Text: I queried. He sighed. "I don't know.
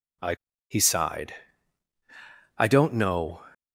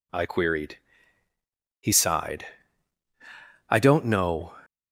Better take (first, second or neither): second